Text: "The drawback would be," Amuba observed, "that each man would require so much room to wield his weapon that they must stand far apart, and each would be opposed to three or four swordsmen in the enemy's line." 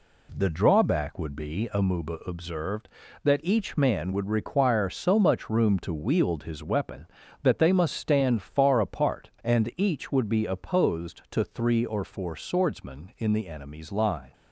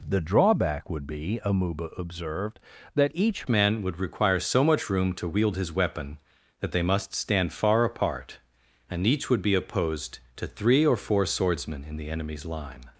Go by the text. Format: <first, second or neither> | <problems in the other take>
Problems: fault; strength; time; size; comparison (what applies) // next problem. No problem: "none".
first | changes voice at "man"; from 3.4 s on; 9.4 s long